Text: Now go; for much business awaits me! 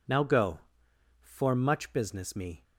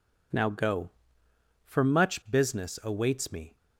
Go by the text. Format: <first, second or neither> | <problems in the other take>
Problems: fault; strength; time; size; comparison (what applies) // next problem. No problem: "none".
second | skips "awaits"; at 2.3 s